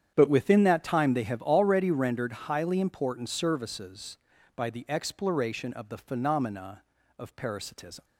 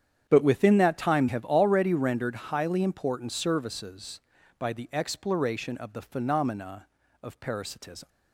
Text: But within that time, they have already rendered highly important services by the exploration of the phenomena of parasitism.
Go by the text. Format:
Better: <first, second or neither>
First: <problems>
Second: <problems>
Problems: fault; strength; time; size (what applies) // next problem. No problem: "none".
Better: first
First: starts louder than the rest; strong; until 1.1 s; 9 dB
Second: starts louder than the rest; strong; until 1.3 s; 9 dB // skips "they"; at 1.2 s